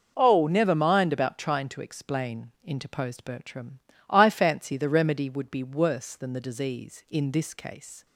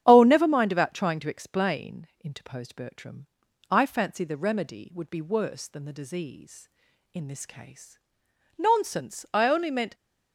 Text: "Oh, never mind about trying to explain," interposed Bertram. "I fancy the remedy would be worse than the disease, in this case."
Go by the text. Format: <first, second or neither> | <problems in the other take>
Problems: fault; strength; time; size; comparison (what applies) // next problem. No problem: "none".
first | starts louder than the rest; strong; until 1.0 s; 9 dB // goes on to say "Nonsense I only meant"; from 8.5 s on; 1.3 s long